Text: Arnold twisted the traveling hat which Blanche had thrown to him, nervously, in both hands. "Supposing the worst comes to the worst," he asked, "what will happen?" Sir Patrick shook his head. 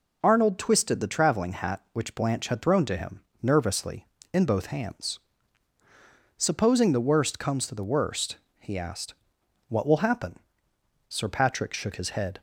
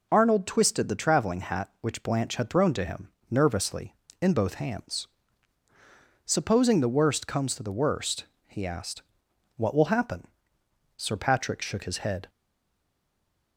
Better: first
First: none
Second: stays silent after the last word; noticeable; from 12.2 s on; 1.3 s long

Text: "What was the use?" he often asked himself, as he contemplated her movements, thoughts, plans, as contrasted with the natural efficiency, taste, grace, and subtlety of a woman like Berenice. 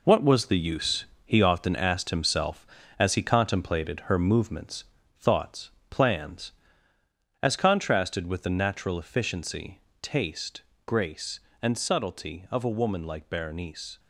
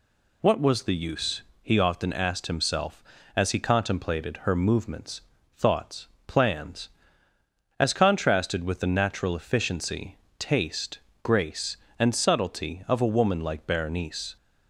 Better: second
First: gets quieter; strong; throughout; 8 dB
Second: none

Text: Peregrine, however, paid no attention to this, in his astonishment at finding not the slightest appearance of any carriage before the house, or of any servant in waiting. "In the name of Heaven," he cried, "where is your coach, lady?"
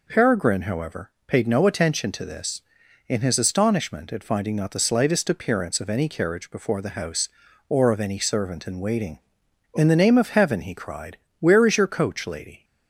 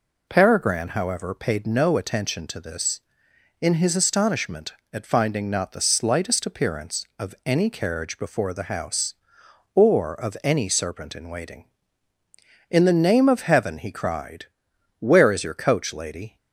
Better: first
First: none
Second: says "serpent" for "servant"; at 10.6 s

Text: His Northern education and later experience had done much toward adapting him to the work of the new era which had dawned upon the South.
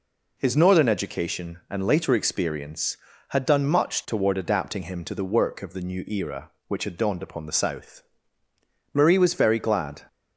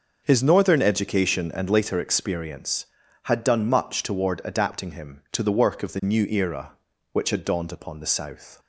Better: second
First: goes on to say "Marie was very glad"; noticeable; from 8.9 s on; 1.1 s long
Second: none

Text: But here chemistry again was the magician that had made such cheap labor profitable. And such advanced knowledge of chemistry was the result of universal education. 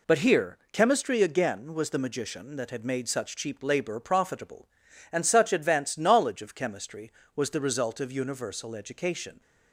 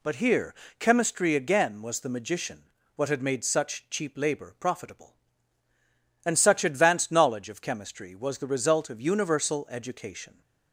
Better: first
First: none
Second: pauses between "here" and "chemistry"; slight; at 0.5 s; 0.24 s long // says "what" for "that"; at 2.9 s

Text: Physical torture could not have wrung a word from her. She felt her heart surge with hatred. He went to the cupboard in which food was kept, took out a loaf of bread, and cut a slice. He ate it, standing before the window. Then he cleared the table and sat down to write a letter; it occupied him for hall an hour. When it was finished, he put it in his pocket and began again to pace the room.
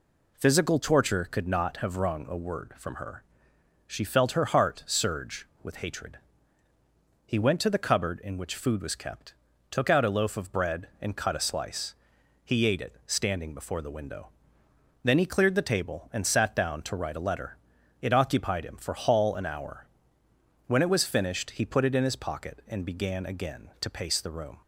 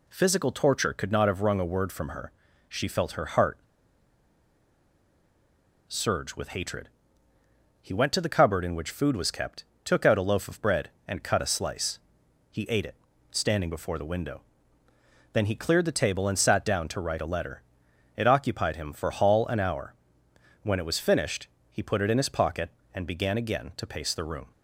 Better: first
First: none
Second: pauses between "heart" and "surge"; strong; at 3.5 s; 2.2 s long

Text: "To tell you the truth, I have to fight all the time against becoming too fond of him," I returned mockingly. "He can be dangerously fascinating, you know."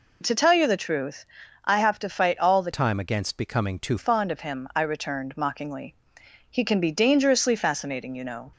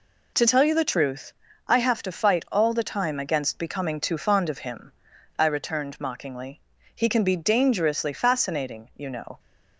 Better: second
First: changes voice from "time" to "too"; from 2.7 to 3.9 s; 1.2 s long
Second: none

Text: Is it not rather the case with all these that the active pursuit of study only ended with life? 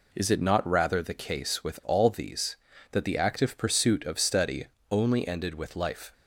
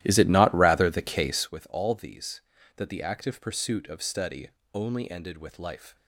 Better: first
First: pauses between "study" and "only"; slight; at 4.6 s; 0.24 s long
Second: starts louder than the rest; strong; until 1.5 s; 14 dB // pauses between "study" and "only"; slight; at 4.4 s; 0.24 s long

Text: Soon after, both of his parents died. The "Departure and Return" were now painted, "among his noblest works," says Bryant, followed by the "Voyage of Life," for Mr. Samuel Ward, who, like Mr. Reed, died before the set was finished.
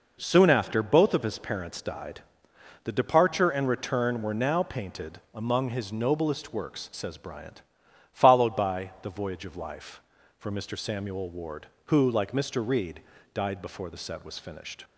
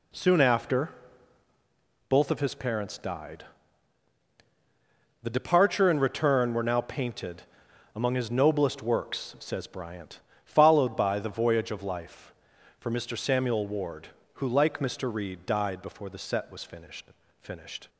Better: first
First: none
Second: says "finished" twice; at 17.4 s

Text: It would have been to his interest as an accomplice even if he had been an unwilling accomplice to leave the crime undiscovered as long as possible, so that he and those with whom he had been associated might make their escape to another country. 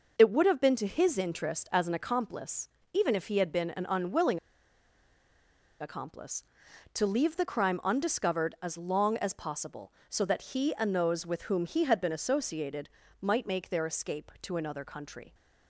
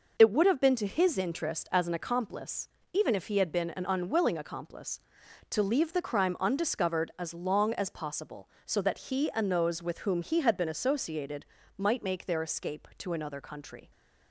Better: second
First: pauses between "accomplice" and "even"; slight; at 2.6 s; 0.24 s long // pauses between "unwilling" and "accomplice"; strong; at 4.3 s; 1.4 s long // pauses between "associated" and "might"; slight; at 12.8 s; 0.32 s long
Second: pauses between "accomplice" and "even"; slight; at 2.6 s; 0.24 s long // pauses between "associated" and "might"; slight; at 11.4 s; 0.32 s long

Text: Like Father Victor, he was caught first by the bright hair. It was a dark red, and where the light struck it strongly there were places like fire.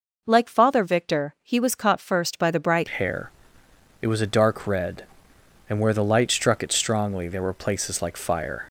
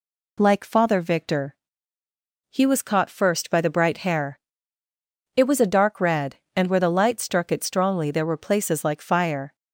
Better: second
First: changes voice at "hair"; from 2.9 s on; 5.7 s long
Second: none

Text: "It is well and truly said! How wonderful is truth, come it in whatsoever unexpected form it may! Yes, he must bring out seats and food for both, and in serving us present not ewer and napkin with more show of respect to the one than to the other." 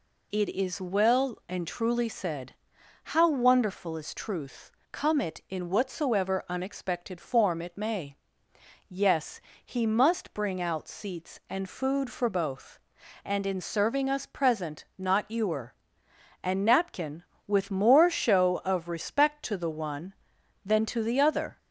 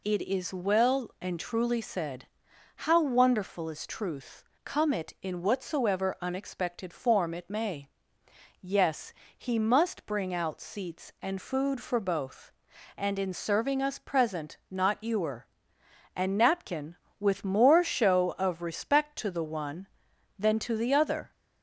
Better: neither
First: none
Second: none

